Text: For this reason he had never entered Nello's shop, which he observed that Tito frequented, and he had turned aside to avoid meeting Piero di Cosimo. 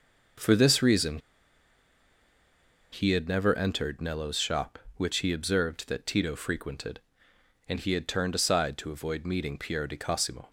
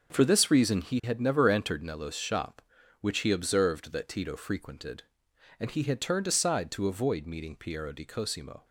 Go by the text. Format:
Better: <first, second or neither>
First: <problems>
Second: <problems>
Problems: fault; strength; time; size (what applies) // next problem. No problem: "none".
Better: second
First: pauses between "reason" and "he"; strong; at 1.1 s; 1.7 s long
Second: none